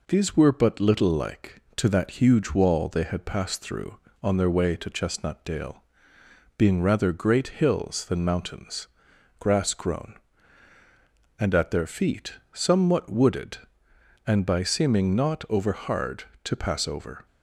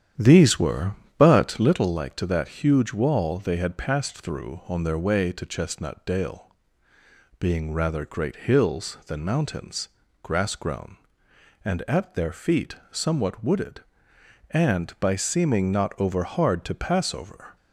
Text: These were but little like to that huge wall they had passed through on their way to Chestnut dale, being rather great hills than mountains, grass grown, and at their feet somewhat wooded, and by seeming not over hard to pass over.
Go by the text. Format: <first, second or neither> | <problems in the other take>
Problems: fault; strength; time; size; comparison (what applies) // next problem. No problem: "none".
first | starts louder than the rest; strong; until 1.8 s; 10 dB // pauses between "feet" and "somewhat"; slight; at 12.7 s; 0.16 s long; slight in the first